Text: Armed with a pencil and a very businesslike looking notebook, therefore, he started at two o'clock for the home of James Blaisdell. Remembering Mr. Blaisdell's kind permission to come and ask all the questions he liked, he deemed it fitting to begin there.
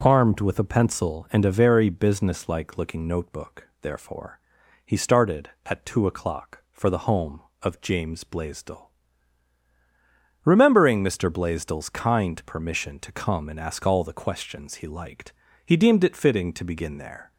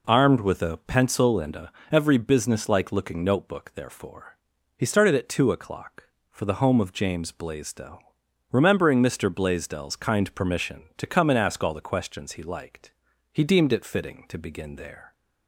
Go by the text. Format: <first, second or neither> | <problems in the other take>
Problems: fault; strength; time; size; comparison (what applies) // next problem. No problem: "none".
first | says "every" for "very"; at 1.9 s